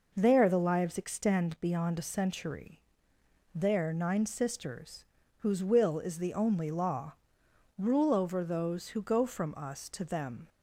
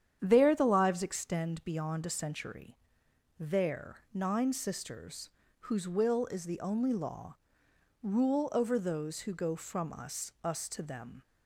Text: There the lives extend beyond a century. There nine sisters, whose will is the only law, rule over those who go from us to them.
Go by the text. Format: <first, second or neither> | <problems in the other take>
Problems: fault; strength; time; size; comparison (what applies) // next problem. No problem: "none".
first | starts louder than the rest; strong; until 1.2 s; 9 dB // says "us" twice; at 10.4 s